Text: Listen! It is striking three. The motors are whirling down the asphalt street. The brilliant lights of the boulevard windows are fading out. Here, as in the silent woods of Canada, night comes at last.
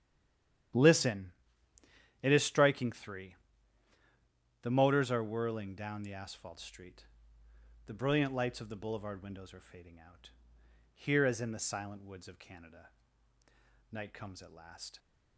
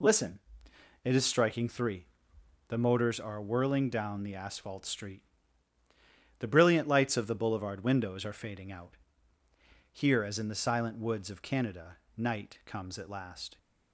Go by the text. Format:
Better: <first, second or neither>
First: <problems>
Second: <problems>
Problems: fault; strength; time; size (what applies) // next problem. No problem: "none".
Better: second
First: stays silent before the first word; slight; until 0.7 s; 0.7 s long // starts louder than the rest; strong; until 2.6 s; 11 dB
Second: none